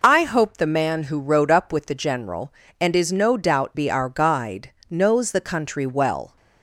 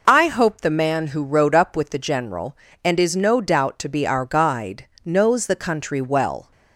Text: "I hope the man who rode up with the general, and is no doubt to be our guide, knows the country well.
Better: second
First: skips "to"; at 3.7 s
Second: none

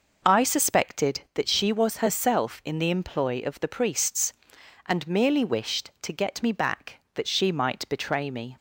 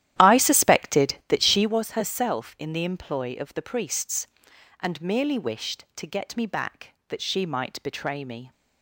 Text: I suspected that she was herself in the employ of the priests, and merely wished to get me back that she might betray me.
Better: first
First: none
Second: starts louder than the rest; strong; until 1.8 s; 12.5 dB

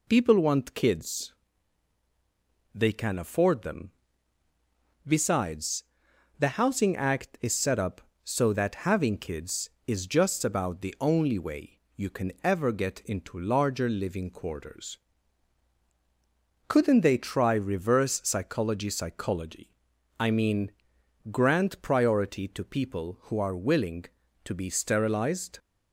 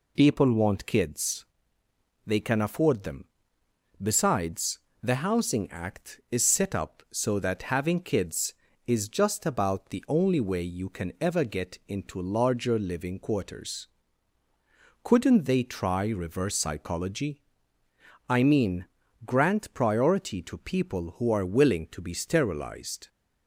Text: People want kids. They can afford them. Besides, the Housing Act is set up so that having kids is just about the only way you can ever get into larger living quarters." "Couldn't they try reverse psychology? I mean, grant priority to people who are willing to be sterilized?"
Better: second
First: pauses between "way" and "you"; slight; at 11.8 s; 0.16 s long // says "psychology" twice; at 18.8 s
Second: none

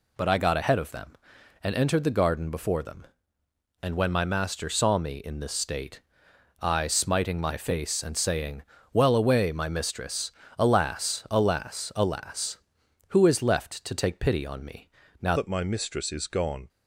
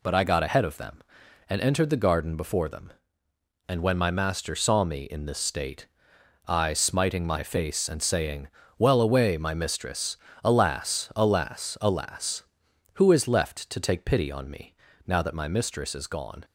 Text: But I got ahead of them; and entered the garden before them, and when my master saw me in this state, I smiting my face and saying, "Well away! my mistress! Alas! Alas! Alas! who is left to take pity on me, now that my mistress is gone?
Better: second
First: changes voice at "that"; from 15.3 s on; 1.3 s long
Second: none

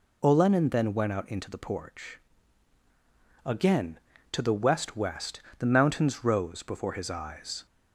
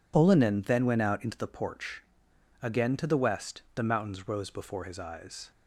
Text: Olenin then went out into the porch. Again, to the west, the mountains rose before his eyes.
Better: second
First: says "west" twice; at 4.9 s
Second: none

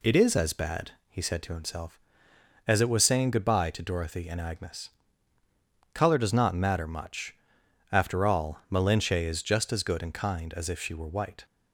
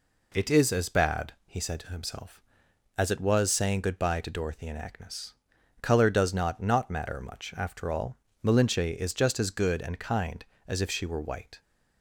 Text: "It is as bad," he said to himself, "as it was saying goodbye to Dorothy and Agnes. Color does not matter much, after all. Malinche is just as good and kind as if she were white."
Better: first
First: none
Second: says "not" twice; at 6.5 s

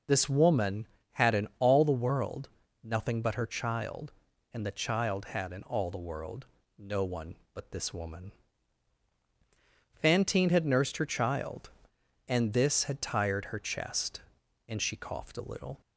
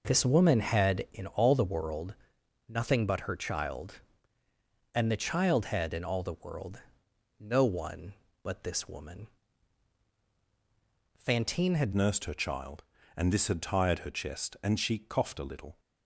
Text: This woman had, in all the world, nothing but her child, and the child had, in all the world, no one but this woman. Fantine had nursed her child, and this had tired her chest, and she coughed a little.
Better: first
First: none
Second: changes voice at "nursed"; from 11.9 s on; 3.8 s long

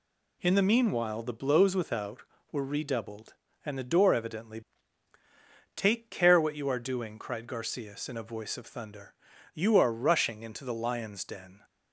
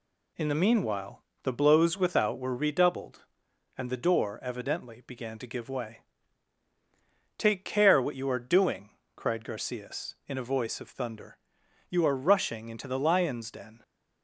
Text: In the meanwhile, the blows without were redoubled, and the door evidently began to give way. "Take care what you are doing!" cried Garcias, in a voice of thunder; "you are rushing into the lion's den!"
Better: second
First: skips "began to give way"; at 5.1 s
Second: none

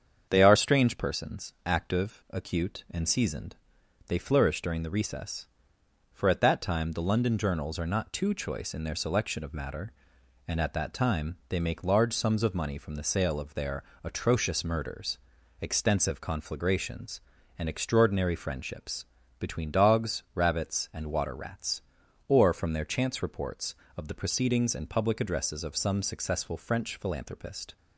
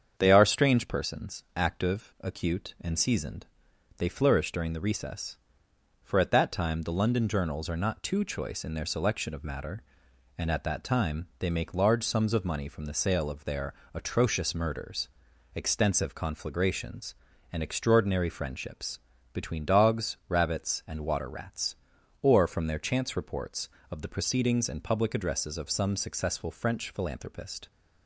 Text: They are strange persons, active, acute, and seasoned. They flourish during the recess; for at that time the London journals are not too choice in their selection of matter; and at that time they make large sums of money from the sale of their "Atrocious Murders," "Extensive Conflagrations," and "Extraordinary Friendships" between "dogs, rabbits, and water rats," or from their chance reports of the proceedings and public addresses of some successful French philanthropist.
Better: neither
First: starts louder than the rest; strong; until 1.3 s; 7.5 dB // pauses between "their" and "Atrocious"; slight; at 13.8 s; 0.18 s long // pauses between "Friendships" and "between"; slight; at 19.0 s; 0.34 s long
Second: starts louder than the rest; strong; until 1.1 s; 7.5 dB // pauses between "their" and "Atrocious"; slight; at 13.7 s; 0.18 s long // pauses between "Friendships" and "between"; slight; at 18.9 s; 0.34 s long

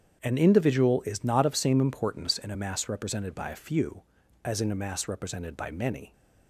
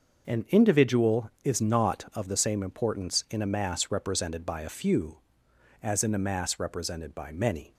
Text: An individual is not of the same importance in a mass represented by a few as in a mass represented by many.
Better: second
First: starts louder than the rest; strong; until 1.2 s; 8 dB // skips "the"; at 1.5 s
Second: starts louder than the rest; until 1.4 s; 6 dB

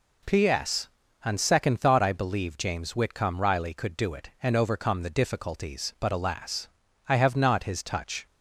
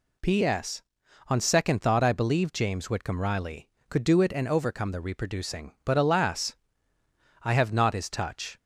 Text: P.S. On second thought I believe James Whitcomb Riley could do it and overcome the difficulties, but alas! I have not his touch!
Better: first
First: none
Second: says "reproducing" for "difficulties"; at 4.9 s

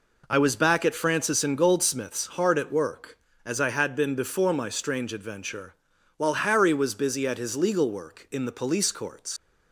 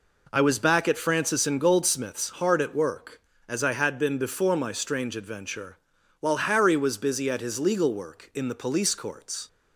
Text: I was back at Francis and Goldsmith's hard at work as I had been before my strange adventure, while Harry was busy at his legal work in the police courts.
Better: second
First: leaves "courts" unfinished; at 9.3 s; 80 ms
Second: none

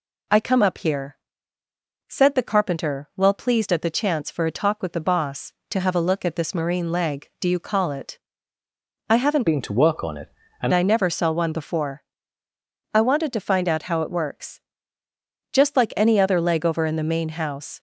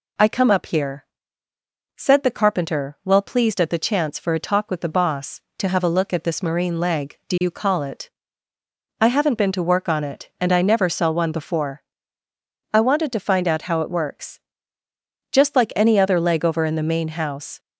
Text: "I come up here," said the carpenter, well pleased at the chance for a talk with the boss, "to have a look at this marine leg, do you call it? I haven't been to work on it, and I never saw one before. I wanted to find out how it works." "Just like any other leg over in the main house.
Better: second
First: changes voice from "been" to "and"; from 9.4 to 10.7 s; 1.3 s long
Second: none

